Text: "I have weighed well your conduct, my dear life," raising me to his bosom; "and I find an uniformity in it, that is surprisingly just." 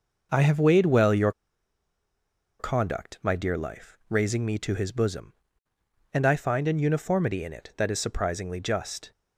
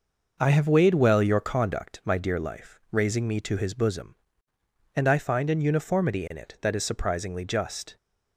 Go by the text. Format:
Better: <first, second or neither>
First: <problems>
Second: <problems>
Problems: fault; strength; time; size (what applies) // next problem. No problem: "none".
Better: second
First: pauses between "your" and "conduct"; strong; at 1.3 s; 1.2 s long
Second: none